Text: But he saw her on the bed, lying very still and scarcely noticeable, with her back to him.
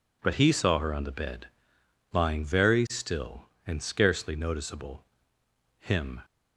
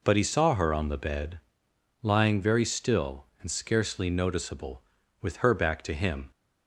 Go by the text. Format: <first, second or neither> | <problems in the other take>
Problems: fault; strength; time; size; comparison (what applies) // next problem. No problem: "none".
second | skips "with her back to"; at 5.4 s